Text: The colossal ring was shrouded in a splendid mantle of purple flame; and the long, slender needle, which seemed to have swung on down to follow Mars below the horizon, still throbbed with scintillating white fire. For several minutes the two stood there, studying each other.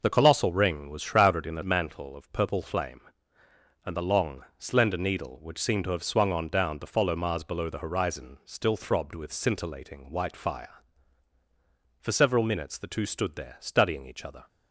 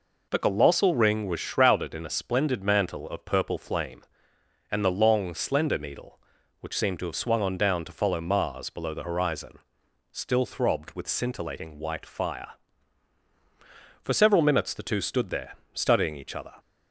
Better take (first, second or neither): second